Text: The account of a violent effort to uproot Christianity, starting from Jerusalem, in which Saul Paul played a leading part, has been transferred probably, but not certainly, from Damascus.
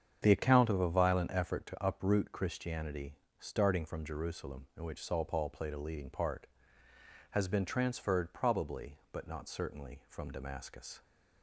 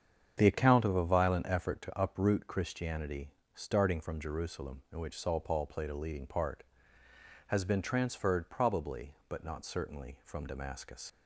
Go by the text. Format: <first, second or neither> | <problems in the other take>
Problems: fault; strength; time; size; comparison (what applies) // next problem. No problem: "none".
first | starts louder than the rest; strong; until 1.3 s; 8 dB; strong in the first // leaves "Damascus" unfinished; at 11.0 s; 70 ms